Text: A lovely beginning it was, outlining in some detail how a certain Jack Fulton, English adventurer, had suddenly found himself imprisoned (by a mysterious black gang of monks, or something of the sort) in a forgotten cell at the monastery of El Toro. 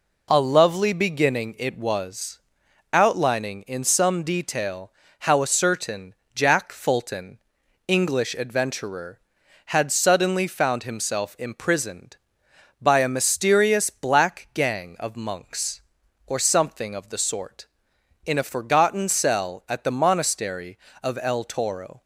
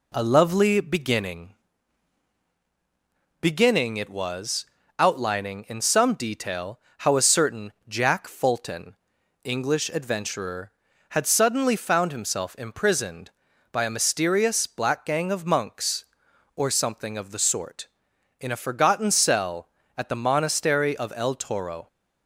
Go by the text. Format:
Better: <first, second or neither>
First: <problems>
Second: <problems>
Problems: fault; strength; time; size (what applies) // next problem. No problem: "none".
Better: first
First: pauses between "detail" and "how"; slight; at 4.9 s; 0.28 s long // pauses between "certain" and "Jack"; slight; at 6.1 s; 0.22 s long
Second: says "beginning" twice; at 3.4 s // pauses between "detail" and "how"; slight; at 6.7 s; 0.20 s long // pauses between "certain" and "Jack"; slight; at 7.7 s; 0.16 s long